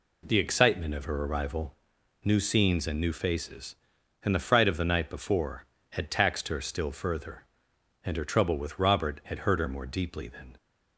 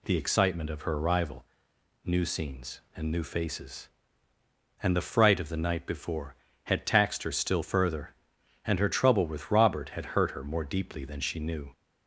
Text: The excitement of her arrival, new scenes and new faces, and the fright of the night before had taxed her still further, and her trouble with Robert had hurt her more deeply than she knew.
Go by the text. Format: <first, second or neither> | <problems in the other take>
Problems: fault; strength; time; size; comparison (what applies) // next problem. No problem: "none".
second | stops before "she knew"; at 10.5 s